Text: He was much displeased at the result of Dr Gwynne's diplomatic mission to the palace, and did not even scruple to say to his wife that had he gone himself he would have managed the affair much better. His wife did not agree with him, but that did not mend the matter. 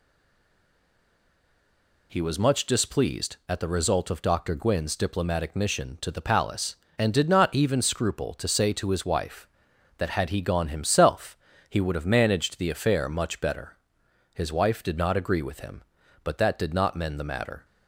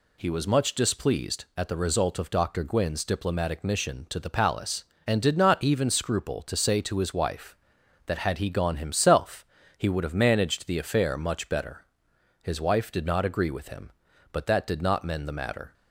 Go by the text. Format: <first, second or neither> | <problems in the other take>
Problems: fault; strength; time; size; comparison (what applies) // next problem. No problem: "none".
second | stays silent before the first word; noticeable; until 2.1 s; 2.1 s long // pauses between "himself" and "he"; slight; at 11.3 s; 0.32 s long; slight in the second